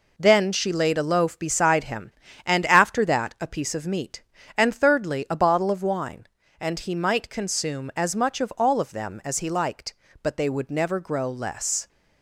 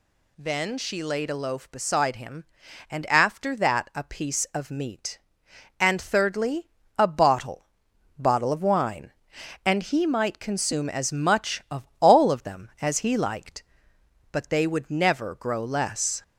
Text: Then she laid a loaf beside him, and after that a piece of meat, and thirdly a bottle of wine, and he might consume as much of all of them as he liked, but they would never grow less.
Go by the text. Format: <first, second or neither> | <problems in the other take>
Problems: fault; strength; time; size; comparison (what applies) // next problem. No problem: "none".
first | pauses between "thirdly" and "a"; slight; at 6.6 s; 0.28 s long // says "bottle" twice; at 8.1 s